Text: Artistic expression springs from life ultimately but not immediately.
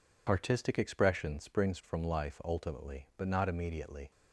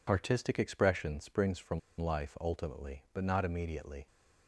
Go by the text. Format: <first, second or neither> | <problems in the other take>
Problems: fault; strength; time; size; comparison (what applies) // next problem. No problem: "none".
first | pauses between "from" and "life"; slight; at 1.7 s; 0.20 s long